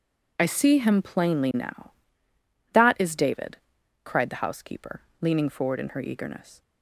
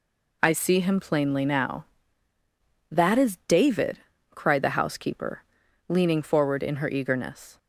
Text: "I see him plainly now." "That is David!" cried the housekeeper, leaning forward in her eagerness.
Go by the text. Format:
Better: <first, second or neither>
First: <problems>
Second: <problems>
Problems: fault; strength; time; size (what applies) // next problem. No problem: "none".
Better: neither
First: none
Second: none